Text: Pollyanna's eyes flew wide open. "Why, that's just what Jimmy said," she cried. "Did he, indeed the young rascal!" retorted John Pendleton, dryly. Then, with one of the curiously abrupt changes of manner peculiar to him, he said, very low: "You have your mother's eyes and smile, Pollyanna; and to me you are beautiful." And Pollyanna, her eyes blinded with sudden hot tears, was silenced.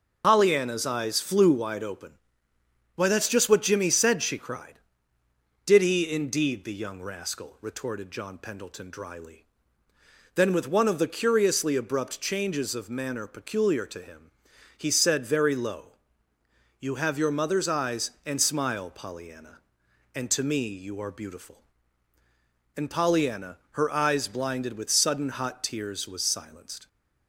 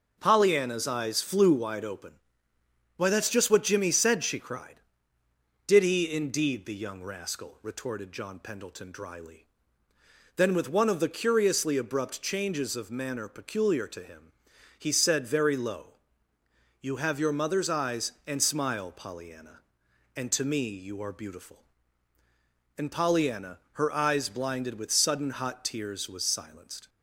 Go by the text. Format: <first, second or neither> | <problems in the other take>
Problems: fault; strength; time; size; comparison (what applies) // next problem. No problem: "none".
second | loses the start of "Pollyanna's"; at 0.2 s; 70 ms // starts louder than the rest; noticeable; until 1.2 s; 6 dB; noticeable in the second